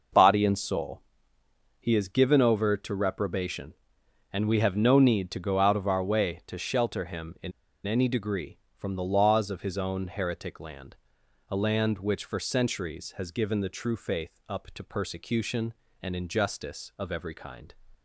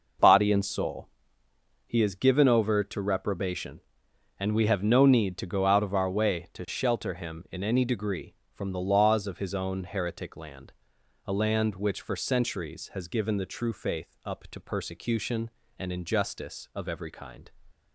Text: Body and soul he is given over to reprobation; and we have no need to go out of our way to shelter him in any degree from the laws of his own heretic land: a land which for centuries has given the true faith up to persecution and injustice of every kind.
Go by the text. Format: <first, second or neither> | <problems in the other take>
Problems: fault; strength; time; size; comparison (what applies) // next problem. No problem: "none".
second | pauses between "soul" and "he"; noticeable; at 1.0 s; 0.78 s long; noticeable in the second // pauses between "in" and "any"; slight; at 7.5 s; 0.34 s long